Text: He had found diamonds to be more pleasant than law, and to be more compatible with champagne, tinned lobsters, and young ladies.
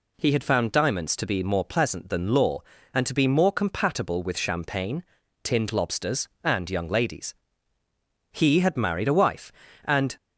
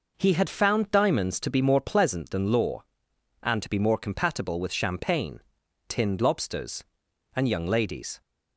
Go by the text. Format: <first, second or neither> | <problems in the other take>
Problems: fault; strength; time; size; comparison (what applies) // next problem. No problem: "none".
second | goes on to say "He had married a wife and"; strong; from 8.3 s on; 1.8 s long